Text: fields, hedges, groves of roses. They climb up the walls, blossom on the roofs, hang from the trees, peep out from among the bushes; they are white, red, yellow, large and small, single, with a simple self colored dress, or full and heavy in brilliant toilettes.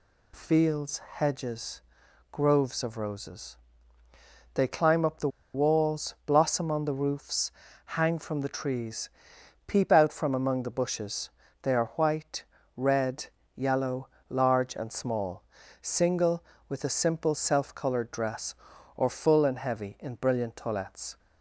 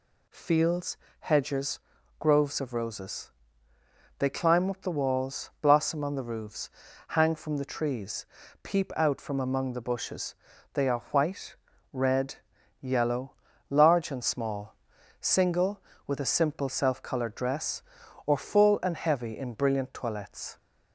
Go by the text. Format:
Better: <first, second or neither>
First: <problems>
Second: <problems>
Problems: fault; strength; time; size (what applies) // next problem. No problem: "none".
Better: second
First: pauses between "the" and "walls"; slight; at 5.2 s; 0.25 s long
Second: none